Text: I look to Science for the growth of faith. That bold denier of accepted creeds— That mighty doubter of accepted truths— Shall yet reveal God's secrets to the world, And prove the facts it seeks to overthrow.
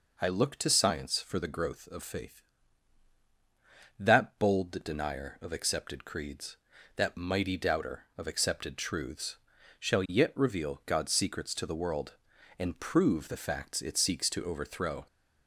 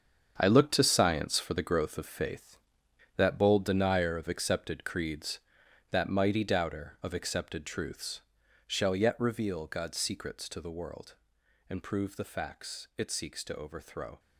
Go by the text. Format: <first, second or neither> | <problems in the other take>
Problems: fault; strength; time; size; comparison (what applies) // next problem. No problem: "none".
first | gets quieter; strong; throughout; 11 dB